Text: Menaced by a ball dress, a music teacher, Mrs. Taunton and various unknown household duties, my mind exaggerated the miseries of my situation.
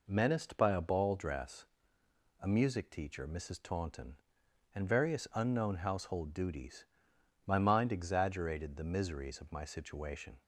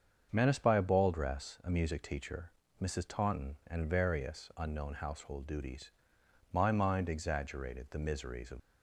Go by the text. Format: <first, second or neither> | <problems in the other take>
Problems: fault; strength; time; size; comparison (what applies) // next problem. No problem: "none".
first | starts louder than the rest; until 1.3 s; 7 dB // stops before "my situation"; at 8.5 s